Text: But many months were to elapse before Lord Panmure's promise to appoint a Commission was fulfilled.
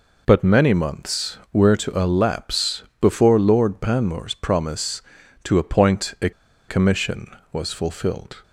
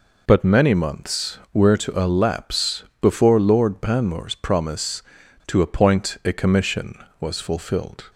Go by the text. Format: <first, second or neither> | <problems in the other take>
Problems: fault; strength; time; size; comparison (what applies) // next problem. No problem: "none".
second | pauses between "elapse" and "before"; slight; at 2.8 s; 0.18 s long; slight in the second // pauses between "a" and "Commission"; at 6.3 s; 0.37 s long